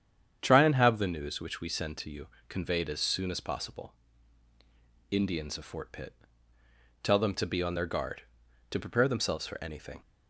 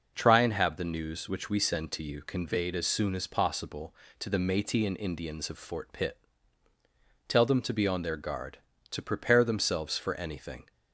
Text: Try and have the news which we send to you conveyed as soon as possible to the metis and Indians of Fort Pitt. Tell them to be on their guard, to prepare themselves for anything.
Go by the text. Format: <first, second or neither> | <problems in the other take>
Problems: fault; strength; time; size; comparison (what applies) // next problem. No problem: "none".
second | starts louder than the rest; strong; until 1.4 s; 8.5 dB // pauses between "you" and "conveyed"; slight; at 2.2 s; 0.20 s long // skips "to the metis and"; at 4.5 s